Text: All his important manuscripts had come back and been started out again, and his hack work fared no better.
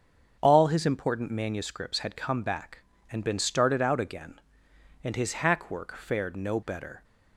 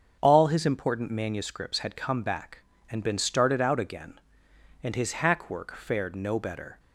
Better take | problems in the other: neither | starts louder than the rest; the same in both

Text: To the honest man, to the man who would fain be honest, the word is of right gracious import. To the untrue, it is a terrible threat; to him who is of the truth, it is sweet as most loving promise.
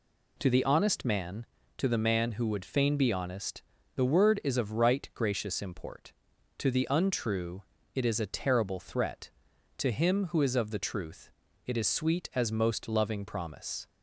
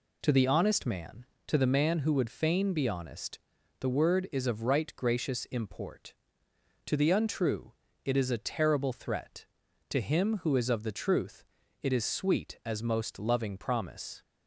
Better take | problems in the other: neither | none

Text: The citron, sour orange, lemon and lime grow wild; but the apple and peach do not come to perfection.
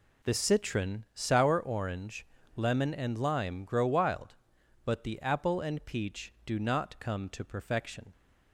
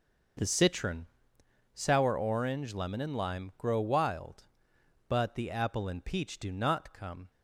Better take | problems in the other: first | starts louder than the rest; noticeable; until 2.0 s; 6 dB // stops before "to perfection"; at 7.3 s

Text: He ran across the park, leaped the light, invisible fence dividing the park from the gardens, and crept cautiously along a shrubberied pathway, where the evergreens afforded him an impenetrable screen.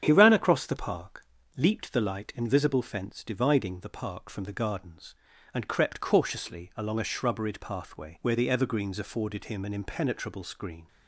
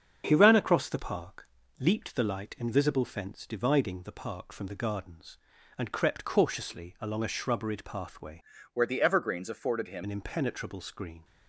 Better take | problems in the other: first | starts louder than the rest; strong; until 1.2 s; 7 dB; strong in the first // changes voice from "where" to "him"; from 8.7 to 10.0 s; 1.3 s long

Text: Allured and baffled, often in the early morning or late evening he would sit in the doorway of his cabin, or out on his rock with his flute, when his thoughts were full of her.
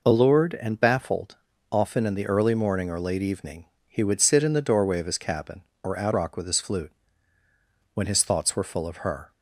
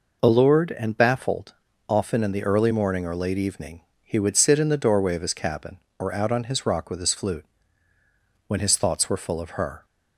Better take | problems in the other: second | pauses between "evening" and "he"; slight; at 3.6 s; 0.20 s long; slight in the second // skips "on his"; at 6.1 s

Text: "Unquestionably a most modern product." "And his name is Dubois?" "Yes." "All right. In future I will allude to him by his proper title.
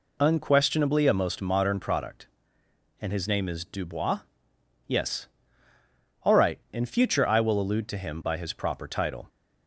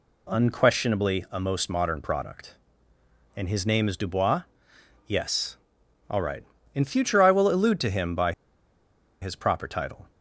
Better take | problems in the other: first | pauses between "by" and "his"; noticeable; at 8.3 s; 0.87 s long

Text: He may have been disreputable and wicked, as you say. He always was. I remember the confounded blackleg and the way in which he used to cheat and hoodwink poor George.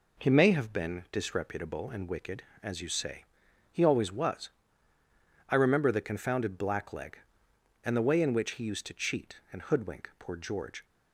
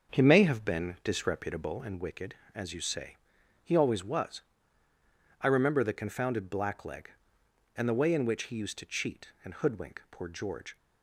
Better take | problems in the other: first | starts louder than the rest; until 1.9 s; 7 dB

